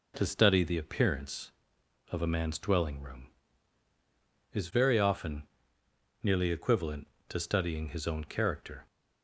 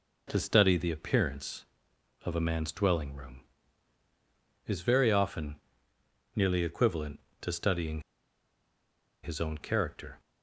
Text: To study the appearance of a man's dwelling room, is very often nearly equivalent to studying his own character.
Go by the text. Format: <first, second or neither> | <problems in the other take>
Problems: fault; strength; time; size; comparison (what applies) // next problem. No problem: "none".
first | pauses between "often" and "nearly"; noticeable; at 5.5 s; 0.80 s long; noticeable in the first // pauses between "studying" and "his"; at 8.0 s; 1.2 s long